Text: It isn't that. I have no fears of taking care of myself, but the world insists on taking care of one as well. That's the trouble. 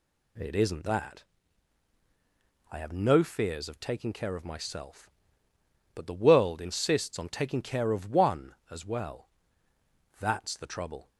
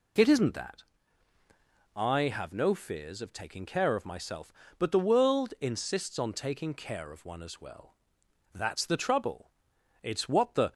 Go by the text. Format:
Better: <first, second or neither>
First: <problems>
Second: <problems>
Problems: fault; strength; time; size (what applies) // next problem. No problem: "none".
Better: first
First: none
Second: goes on to say "It's what the"; noticeable; from 10.0 s on; 0.70 s long